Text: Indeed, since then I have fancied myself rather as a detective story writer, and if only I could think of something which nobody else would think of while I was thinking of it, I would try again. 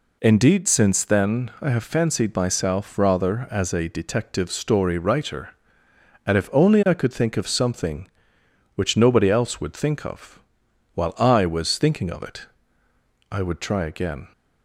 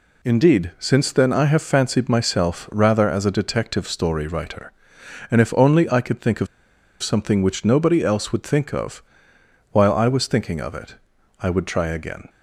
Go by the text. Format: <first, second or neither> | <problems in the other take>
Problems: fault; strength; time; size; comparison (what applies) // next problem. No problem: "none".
first | pauses between "of" and "something"; noticeable; at 6.4 s; 0.56 s long // pauses between "of" and "while"; noticeable; at 9.0 s; 0.68 s long; noticeable in the first